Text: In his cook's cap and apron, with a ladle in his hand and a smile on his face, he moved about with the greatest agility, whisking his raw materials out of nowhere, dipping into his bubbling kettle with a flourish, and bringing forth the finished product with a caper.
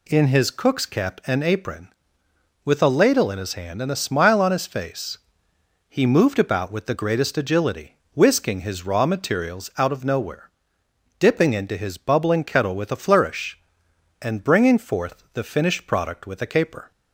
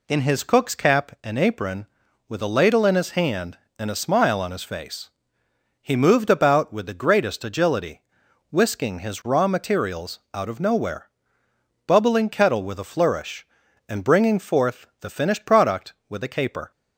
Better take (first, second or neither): first